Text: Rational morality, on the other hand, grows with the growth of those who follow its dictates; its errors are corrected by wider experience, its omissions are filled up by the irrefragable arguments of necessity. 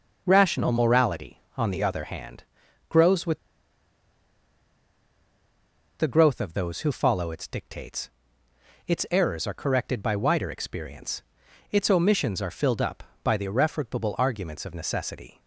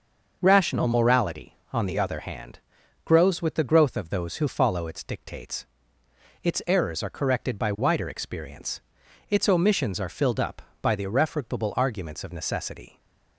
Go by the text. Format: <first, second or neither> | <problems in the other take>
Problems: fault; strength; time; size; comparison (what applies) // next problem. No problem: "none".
second | starts louder than the rest; until 1.2 s; 6 dB; also in the second // pauses between "with" and "the"; strong; at 3.3 s; 2.6 s long